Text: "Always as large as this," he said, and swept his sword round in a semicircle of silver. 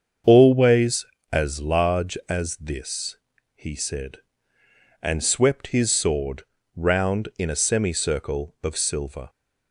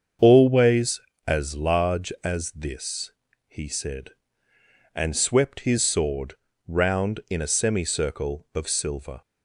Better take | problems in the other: neither | starts louder than the rest; the same in both // pauses between "sword" and "round"; slight; the same in both

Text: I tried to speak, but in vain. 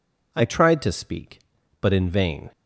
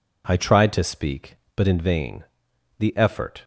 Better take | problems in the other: first | goes on to say "The effort"; noticeable; from 2.7 s on; 0.64 s long

